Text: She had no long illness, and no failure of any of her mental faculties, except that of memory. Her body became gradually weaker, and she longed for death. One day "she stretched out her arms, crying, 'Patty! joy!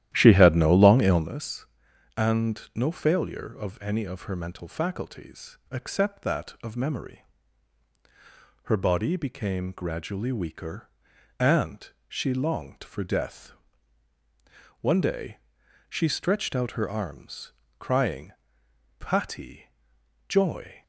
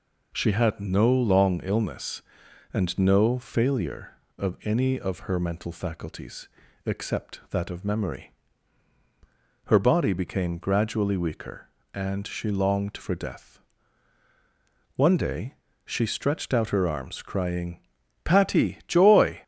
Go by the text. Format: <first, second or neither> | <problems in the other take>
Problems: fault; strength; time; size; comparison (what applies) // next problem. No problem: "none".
second | starts louder than the rest; strong; until 1.3 s; 12.5 dB // pauses between "and" and "she"; slight; at 11.8 s; 0.18 s long // pauses between "day" and "she"; noticeable; at 15.3 s; 0.50 s long; slight in the second